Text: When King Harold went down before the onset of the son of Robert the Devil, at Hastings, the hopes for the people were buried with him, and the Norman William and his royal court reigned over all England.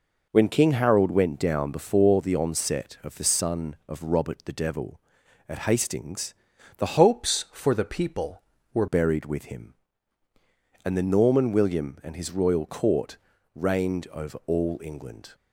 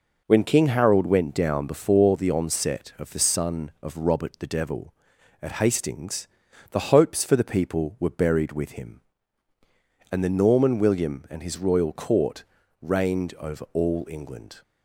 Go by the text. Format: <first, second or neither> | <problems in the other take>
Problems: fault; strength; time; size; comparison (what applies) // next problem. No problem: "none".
second | changes voice from "hopes" to "were"; from 6.9 to 8.8 s; 1.9 s long // pauses between "court" and "reigned"; at 13.1 s; 0.38 s long; also in the second